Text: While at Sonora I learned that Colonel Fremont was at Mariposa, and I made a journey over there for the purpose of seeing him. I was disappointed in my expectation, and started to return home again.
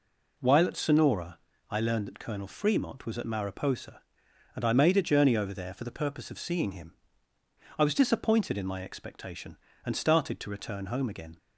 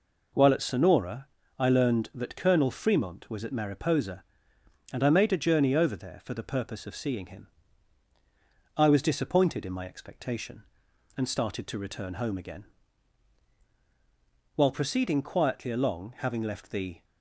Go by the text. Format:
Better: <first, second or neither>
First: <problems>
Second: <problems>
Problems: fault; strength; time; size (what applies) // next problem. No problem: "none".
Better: first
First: pauses between "Sonora" and "I"; slight; at 1.3 s; 0.32 s long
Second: pauses between "Sonora" and "I"; slight; at 1.2 s; 0.30 s long // goes on to say "While proceeding quietly along having left the"; strong; from 14.5 s on; 2.4 s long